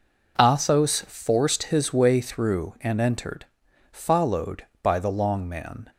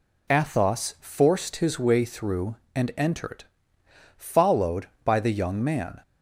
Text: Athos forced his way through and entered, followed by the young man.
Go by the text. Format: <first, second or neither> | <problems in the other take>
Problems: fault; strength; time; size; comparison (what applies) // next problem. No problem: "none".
second | says "long" for "young"; at 5.1 s